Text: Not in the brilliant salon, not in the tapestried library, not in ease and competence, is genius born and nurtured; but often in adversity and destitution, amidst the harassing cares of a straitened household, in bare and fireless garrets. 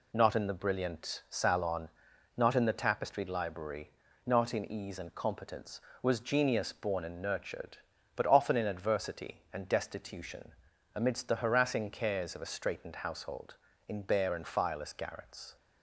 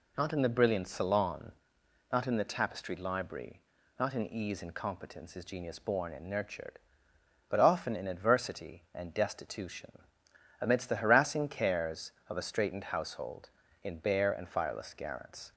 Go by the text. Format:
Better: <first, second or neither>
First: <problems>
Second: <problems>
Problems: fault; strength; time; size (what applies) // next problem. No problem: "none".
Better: second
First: says "was" for "is"; at 6.0 s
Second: none